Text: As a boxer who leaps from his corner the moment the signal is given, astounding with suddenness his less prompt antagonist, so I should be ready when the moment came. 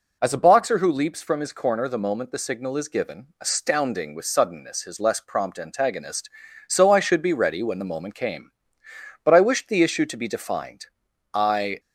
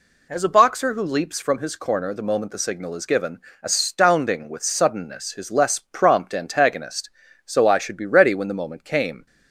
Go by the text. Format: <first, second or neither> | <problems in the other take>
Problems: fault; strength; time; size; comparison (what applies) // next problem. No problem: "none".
second | goes on to say "But I wished the issue to be defined I"; strong; from 9.2 s on; 2.5 s long